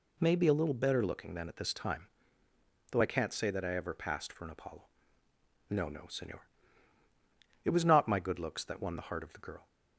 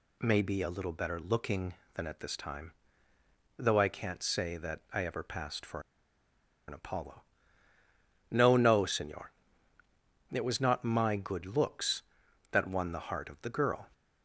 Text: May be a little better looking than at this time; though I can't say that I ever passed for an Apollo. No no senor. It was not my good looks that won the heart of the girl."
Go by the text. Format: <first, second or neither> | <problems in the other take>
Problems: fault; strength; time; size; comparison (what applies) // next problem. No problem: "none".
first | pauses between "for" and "an"; noticeable; at 5.7 s; 0.88 s long